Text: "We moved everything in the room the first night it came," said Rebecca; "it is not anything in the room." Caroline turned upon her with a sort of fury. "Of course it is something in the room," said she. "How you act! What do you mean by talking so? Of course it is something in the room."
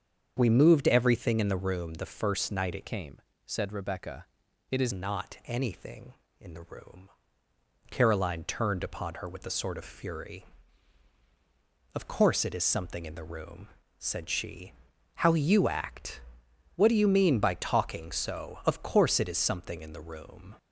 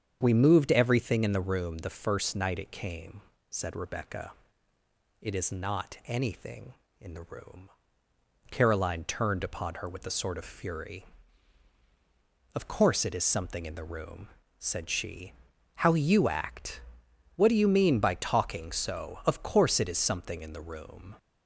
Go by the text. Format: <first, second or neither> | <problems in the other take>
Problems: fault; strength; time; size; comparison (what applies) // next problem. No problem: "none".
second | starts louder than the rest; strong; until 1.3 s; 7.5 dB; strong in the second // changes voice from "came" to "is"; from 2.8 to 4.9 s; 2.1 s long